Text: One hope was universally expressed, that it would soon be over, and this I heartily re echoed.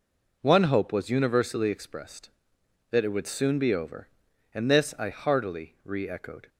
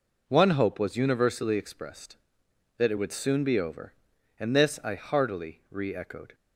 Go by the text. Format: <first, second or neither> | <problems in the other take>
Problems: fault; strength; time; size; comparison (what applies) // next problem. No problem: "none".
neither | none